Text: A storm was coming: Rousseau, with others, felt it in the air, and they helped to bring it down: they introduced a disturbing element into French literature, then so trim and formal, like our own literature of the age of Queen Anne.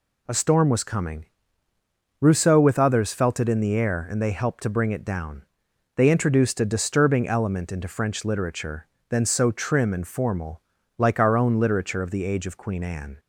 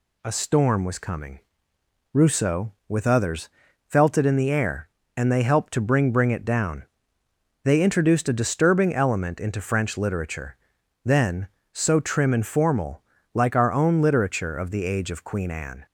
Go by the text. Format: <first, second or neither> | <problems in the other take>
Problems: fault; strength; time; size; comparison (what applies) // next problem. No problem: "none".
first | says "bring" twice; at 6.1 s